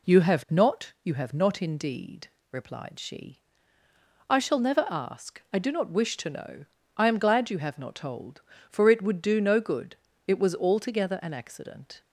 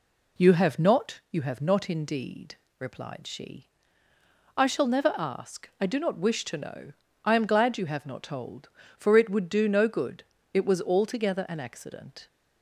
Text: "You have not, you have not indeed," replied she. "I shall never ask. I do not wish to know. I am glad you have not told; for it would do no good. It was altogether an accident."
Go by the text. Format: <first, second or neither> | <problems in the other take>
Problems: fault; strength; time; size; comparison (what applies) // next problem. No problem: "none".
neither | none